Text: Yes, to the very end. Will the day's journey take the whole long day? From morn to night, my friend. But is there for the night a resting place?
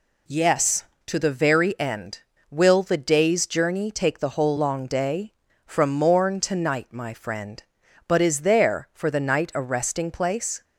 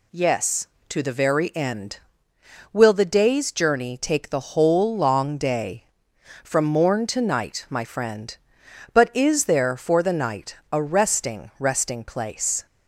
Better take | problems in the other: first | says "resting" twice; at 11.5 s

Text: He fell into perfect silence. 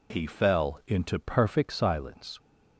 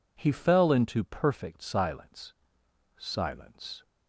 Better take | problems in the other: first | says "silence" twice; at 2.9 s

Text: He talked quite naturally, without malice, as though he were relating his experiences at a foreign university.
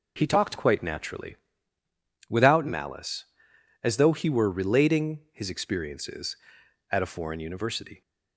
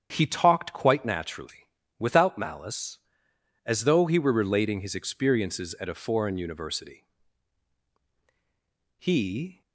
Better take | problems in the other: first | starts louder than the rest; strong; until 1.1 s; 8 dB // goes on to say "He"; noticeable; from 8.9 s on; 0.62 s long

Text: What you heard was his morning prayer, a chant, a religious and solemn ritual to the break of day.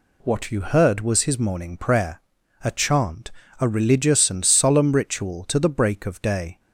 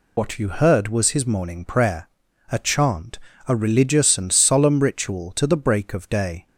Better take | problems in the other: first | loses the start of "What"; at 0.1 s; 95 ms

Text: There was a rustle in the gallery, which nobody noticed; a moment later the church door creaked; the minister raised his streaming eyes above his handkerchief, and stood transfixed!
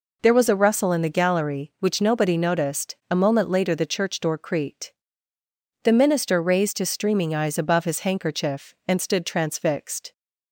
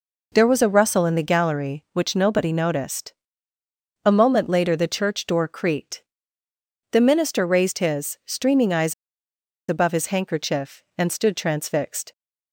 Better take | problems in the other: first | pauses between "eyes" and "above"; noticeable; at 8.9 s; 0.75 s long

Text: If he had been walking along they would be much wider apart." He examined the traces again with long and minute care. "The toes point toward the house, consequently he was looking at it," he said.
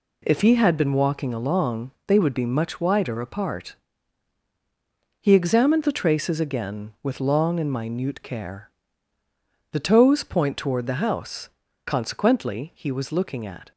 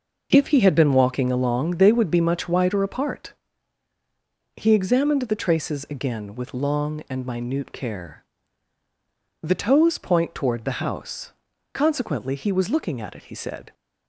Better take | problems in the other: second | pauses between "along" and "they"; slight; at 1.9 s; 0.16 s long // stops before "it he said"; at 13.7 s

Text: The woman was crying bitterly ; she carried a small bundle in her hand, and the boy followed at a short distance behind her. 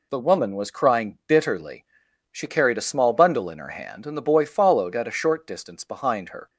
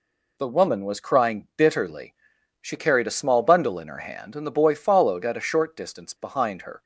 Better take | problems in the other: neither | none

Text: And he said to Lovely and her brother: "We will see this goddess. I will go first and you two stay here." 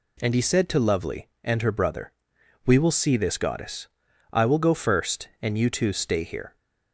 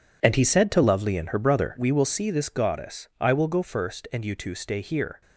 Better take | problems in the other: neither | none

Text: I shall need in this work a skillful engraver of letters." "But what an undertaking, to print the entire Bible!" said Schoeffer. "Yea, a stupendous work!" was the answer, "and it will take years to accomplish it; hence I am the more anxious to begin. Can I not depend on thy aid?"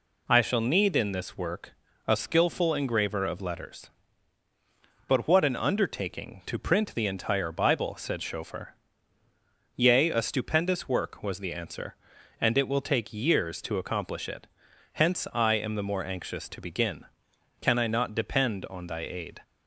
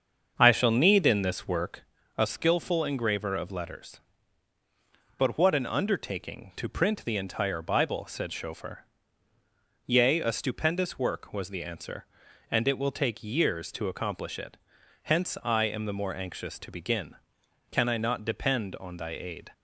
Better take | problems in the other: first | starts louder than the rest; until 1.9 s; 7 dB // pauses between "work" and "a"; slight; at 1.8 s; 0.34 s long; slight in the first

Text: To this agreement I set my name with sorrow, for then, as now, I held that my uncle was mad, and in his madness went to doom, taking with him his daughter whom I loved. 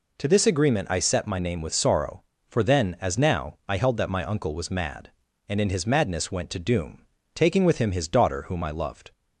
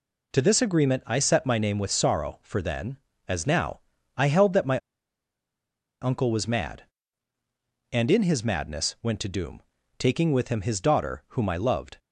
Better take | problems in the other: first | pauses between "my" and "uncle"; at 4.7 s; 1.2 s long

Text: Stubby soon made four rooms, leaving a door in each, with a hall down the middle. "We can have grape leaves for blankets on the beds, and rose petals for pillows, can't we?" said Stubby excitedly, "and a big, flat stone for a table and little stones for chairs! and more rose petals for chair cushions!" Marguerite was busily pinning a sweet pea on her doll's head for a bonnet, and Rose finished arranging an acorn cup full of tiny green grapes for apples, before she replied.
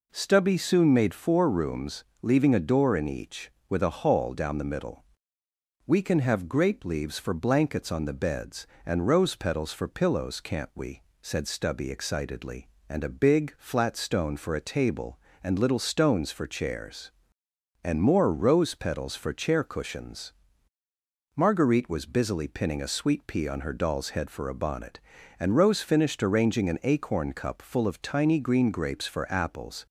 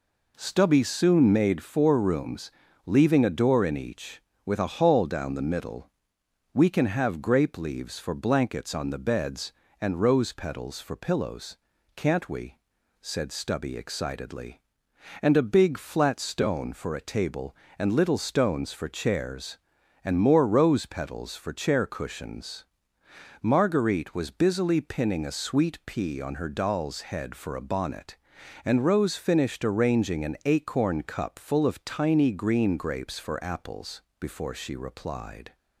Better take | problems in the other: second | stops before "before she replied"; at 29.8 s

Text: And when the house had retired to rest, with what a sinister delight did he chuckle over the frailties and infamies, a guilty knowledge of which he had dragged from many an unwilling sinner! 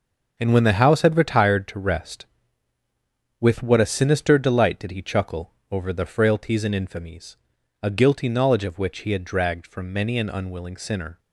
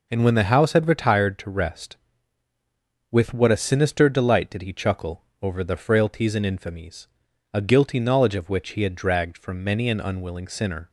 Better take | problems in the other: second | gets quieter; strong; throughout; 9.5 dB // pauses between "chuckle" and "over"; slight; at 5.5 s; 0.20 s long; slight in the second

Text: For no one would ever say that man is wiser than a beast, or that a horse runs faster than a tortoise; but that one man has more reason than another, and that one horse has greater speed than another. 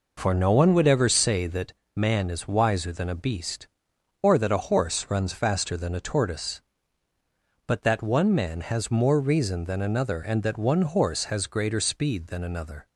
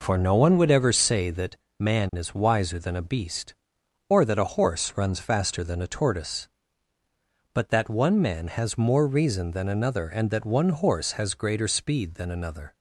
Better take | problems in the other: neither | pauses between "that" and "man"; slight; the same in both

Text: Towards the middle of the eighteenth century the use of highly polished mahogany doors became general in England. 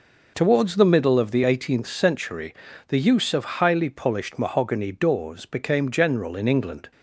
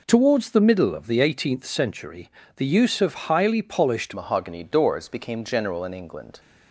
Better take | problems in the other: first | pauses between "century" and "the"; slight; at 2.2 s; 0.28 s long; slight in the first // changes voice at "mahogany"; from 4.1 s on; 2.2 s long

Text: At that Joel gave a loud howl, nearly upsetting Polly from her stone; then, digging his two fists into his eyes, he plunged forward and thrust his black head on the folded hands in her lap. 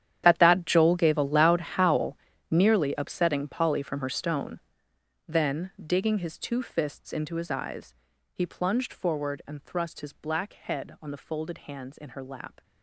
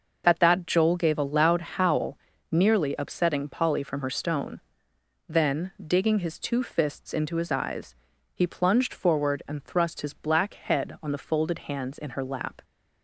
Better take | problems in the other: second | gets quieter; strong; throughout; 17.5 dB

